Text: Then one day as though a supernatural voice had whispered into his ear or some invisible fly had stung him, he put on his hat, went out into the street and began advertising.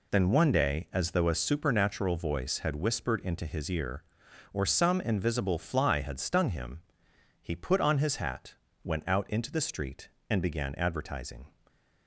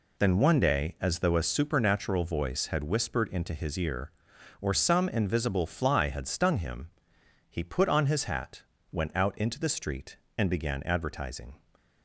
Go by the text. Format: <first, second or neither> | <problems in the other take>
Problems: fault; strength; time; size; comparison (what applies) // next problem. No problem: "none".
neither | none